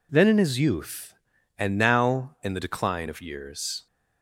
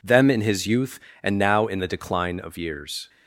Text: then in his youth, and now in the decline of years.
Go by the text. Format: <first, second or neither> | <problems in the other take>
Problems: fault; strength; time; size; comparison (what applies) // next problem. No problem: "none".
first | says "them" for "then"; at 0.0 s